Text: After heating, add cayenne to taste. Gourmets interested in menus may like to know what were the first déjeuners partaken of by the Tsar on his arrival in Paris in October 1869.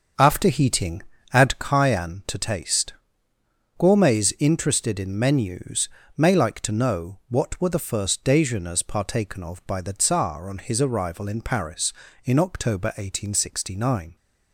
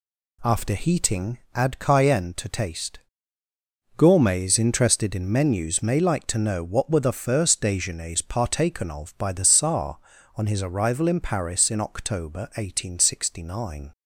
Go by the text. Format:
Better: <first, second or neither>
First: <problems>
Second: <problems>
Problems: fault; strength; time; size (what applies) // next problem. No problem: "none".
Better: second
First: starts louder than the rest; until 1.8 s; 7 dB // pauses between "menus" and "may"; slight; at 5.8 s; 0.26 s long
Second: none